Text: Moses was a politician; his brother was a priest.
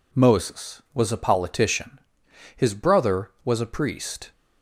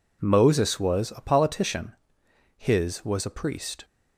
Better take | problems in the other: first | skips "brother"; at 3.0 s

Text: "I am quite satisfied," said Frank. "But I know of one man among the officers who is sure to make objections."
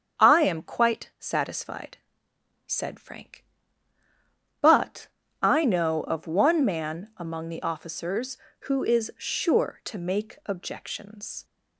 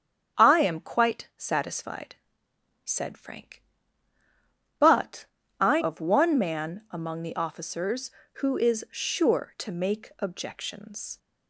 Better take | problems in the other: first | starts louder than the rest; strong; until 1.4 s; 7.5 dB; also in the first // pauses between "But" and "I"; slight; at 5.2 s; 0.34 s long; slight in the first // skips "know"; at 5.8 s

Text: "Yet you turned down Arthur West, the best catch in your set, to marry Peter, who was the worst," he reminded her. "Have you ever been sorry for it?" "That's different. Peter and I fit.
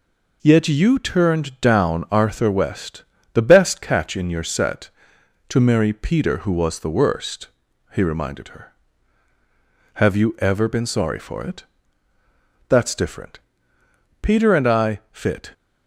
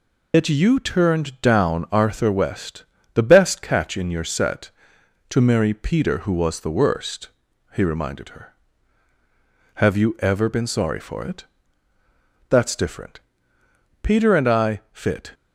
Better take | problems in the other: first | loses the start of "Yet"; at 0.3 s; 125 ms

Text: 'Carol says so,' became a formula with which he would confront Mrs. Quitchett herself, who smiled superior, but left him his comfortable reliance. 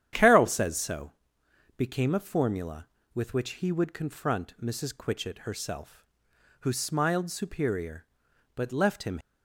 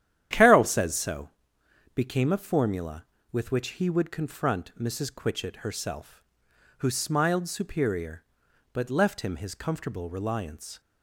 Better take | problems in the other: second | starts louder than the rest; strong; until 1.7 s; 10 dB; strong in the second // stops before "his comfortable reliance"; at 9.1 s

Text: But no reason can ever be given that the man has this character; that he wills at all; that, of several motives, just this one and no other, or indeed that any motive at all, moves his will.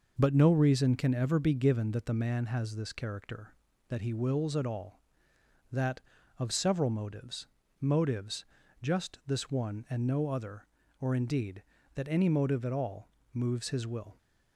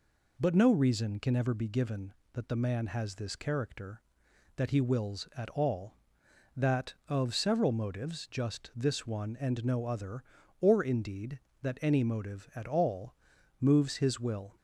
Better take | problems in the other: second | says "motives" twice; at 7.7 s

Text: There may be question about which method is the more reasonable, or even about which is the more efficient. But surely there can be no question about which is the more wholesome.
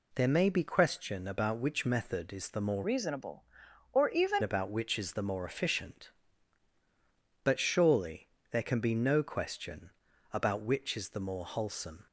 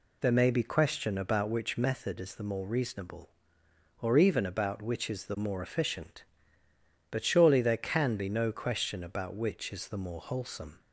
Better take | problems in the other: second | changes voice from "reasonable" to "even"; from 2.8 to 4.4 s; 1.6 s long // pauses between "surely" and "there"; slight; at 8.2 s; 0.22 s long // pauses between "question" and "about"; at 9.9 s; 0.42 s long

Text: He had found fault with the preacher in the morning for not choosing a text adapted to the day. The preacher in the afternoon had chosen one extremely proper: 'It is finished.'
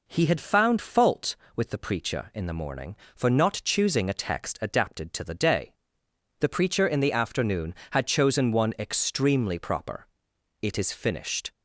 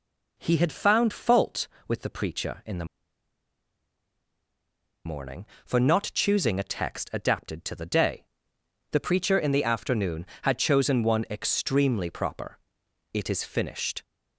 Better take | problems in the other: first | pauses between "the" and "morning"; strong; at 2.8 s; 2.2 s long

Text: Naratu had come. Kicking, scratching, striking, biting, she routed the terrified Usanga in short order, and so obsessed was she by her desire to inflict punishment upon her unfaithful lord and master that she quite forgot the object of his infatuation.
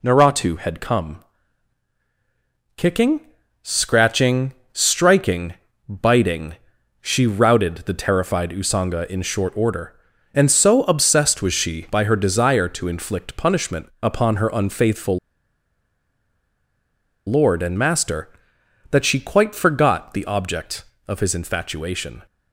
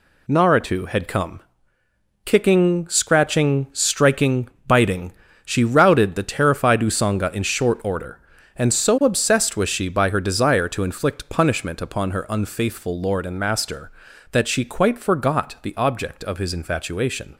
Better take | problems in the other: second | pauses between "unfaithful" and "lord"; strong; at 15.1 s; 2.0 s long

